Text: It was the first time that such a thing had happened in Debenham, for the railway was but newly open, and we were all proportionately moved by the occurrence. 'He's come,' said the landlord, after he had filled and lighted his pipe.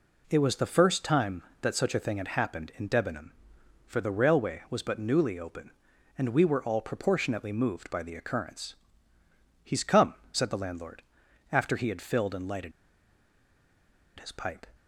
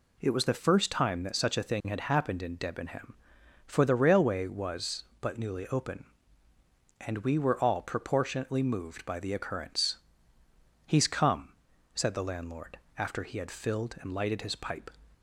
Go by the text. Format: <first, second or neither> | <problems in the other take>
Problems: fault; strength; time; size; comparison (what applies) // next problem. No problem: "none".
second | pauses between "lighted" and "his"; strong; at 12.7 s; 1.4 s long